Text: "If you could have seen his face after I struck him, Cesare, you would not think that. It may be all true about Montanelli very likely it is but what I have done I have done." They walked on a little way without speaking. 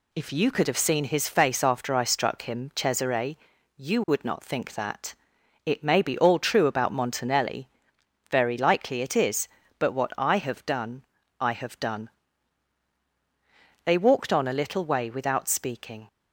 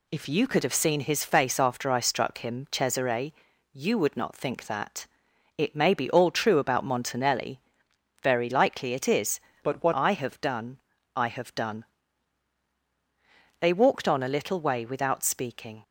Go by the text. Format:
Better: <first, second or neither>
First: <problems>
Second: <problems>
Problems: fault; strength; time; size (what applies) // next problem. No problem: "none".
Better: first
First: pauses between "Montanelli" and "very"; noticeable; at 7.6 s; 0.64 s long // pauses between "done" and "I"; slight; at 11.0 s; 0.36 s long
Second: pauses between "Montanelli" and "very"; noticeable; at 7.5 s; 0.64 s long // changes voice from "but" to "what"; from 9.6 to 9.9 s; 0.3 s long // pauses between "done" and "I"; slight; at 10.7 s; 0.36 s long